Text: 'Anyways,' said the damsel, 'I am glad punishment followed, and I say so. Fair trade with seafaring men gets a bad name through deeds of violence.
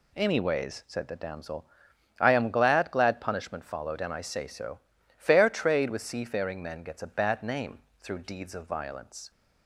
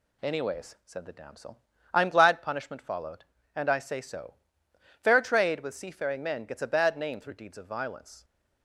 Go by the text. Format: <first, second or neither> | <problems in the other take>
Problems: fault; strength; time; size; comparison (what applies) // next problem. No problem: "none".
second | says "glad" twice; at 2.9 s // pauses between "name" and "through"; slight; at 7.7 s; 0.24 s long